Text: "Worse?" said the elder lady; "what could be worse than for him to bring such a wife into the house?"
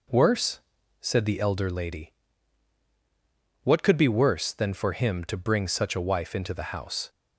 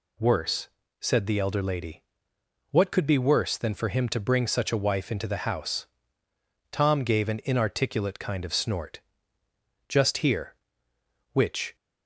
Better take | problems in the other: first | goes on to say "Tom gave an inarticulate kind of snort just here which"; strong; from 6.7 s on; 5.0 s long

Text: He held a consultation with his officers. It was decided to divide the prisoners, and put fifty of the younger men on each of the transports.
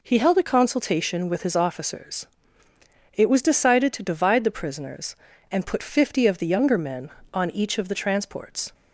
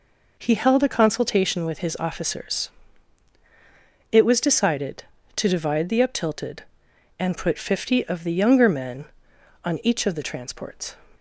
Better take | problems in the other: first | says "uptilted" for "prisoners"; at 6.0 s

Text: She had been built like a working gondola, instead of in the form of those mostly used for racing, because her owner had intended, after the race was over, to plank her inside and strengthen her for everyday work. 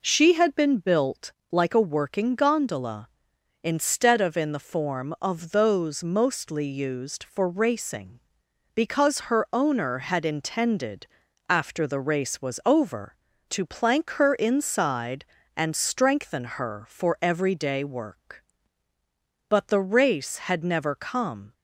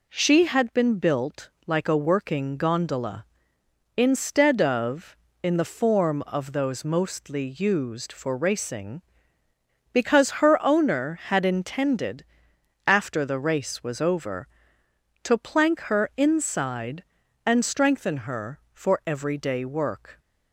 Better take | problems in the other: second | pauses between "built" and "like"; slight; at 1.3 s; 0.20 s long; slight in the second // goes on to say "But the race had never come"; strong; from 19.4 s on; 2.0 s long

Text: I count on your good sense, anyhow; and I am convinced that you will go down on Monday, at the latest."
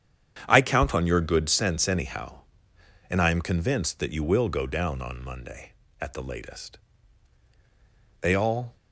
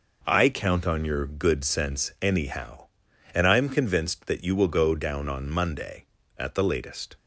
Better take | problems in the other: second | starts louder than the rest; strong; until 1.4 s; 8.5 dB // goes on to say "They all"; from 8.2 s on; 0.54 s long

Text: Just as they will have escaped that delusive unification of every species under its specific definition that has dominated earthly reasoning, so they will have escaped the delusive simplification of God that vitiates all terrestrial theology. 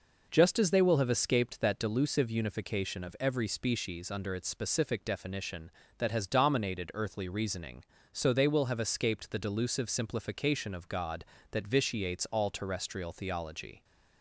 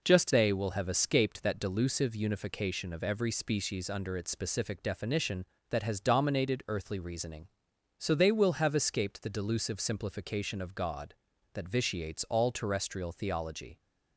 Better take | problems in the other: first | skips "as"; at 0.3 s

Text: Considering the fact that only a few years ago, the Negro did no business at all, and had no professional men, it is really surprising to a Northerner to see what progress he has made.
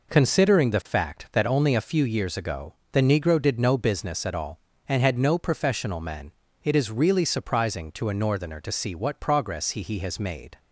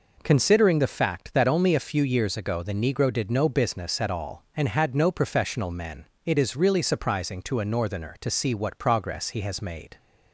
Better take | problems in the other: second | says "he" twice; at 9.8 s

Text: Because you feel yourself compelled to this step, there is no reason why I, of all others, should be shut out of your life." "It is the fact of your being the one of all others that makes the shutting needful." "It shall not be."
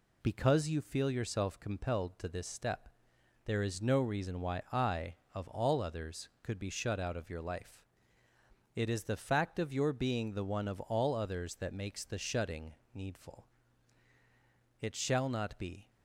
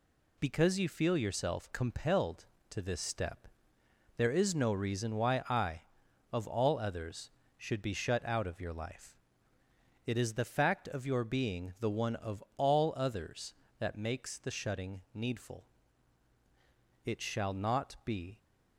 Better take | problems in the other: second | says "could" for "should"; at 6.4 s // pauses between "shutting" and "needful"; slight; at 12.7 s; 0.20 s long

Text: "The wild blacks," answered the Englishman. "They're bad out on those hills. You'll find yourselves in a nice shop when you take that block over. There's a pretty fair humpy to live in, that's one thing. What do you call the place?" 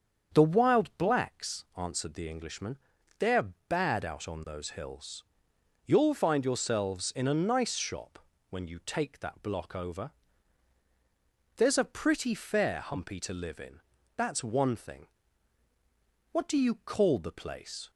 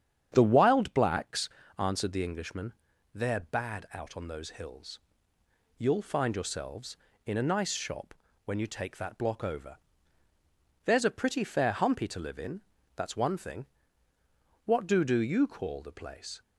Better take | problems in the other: first | starts louder than the rest; strong; until 1.3 s; 9 dB; also in the first // pauses between "shop" and "when"; slight; at 8.1 s; 0.32 s long; slight in the first // says "do" twice; at 15.0 s

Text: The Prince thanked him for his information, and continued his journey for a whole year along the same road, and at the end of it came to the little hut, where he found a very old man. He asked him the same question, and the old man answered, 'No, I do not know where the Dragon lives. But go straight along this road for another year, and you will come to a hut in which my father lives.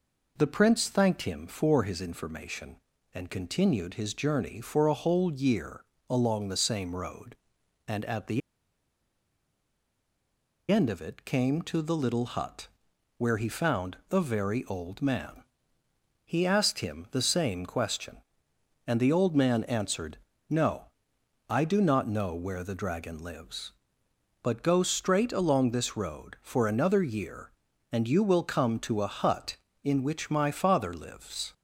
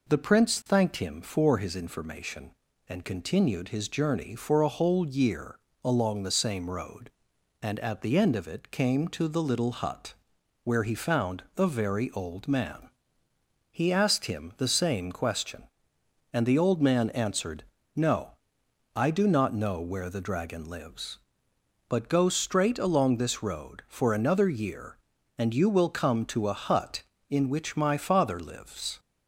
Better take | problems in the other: second | pauses between "year" and "along"; slight; at 5.8 s; 0.28 s long; slight in the second // pauses between "the" and "end"; strong; at 8.4 s; 2.3 s long

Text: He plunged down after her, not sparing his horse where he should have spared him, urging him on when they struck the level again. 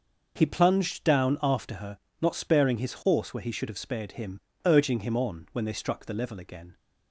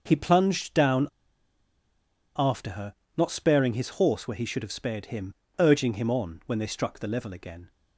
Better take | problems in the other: first | starts louder than the rest; noticeable; until 1.0 s; 6 dB; noticeable in the first // pauses between "down" and "after"; strong; at 1.0 s; 1.2 s long

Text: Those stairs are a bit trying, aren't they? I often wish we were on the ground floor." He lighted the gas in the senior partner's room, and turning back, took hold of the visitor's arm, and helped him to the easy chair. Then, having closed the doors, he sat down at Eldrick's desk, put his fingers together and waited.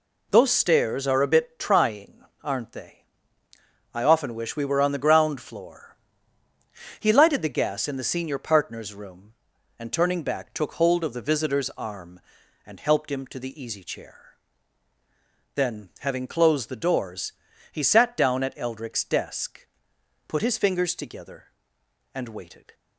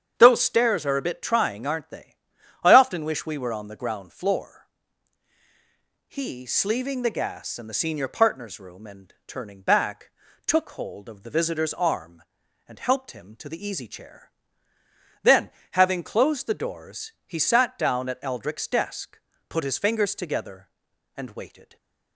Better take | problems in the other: first | starts louder than the rest; strong; until 1.1 s; 8 dB // says "sleeving" for "lighted"; at 6.4 s // stays silent after the last word; slight; from 21.6 s on; 0.5 s long

